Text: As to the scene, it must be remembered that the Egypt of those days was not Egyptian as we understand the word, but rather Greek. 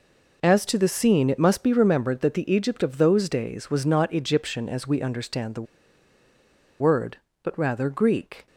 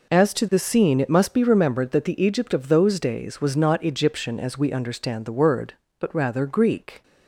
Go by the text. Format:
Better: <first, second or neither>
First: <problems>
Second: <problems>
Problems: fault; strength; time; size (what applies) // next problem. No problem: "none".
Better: second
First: pauses between "the" and "word"; at 5.6 s; 1.1 s long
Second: none